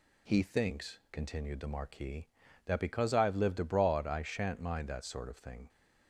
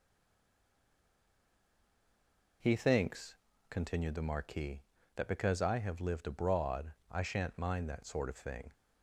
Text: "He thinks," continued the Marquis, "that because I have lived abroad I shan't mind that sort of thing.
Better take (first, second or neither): first